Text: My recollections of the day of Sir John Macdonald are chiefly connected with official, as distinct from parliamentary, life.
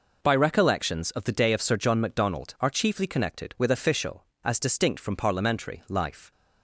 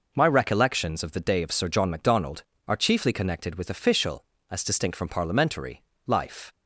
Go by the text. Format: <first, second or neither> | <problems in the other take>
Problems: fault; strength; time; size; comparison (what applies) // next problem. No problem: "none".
second | says "By" for "My"; at 0.2 s